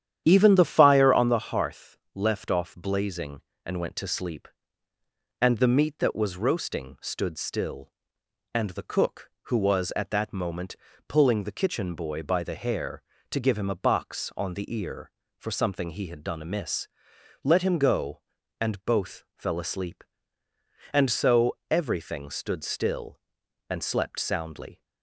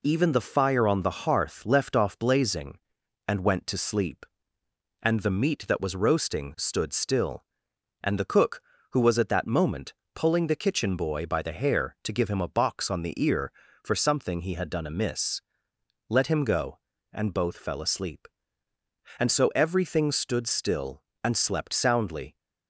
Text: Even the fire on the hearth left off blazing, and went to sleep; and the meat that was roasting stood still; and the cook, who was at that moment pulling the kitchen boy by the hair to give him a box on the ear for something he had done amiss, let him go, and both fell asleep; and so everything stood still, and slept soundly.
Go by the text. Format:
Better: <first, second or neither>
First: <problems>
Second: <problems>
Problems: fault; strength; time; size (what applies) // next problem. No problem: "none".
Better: second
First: starts louder than the rest; strong; until 1.4 s; 10 dB // pauses between "hearth" and "left"; slight; at 1.9 s; 0.18 s long // pauses between "moment" and "pulling"; slight; at 10.7 s; 0.32 s long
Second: pauses between "moment" and "pulling"; slight; at 9.9 s; 0.18 s long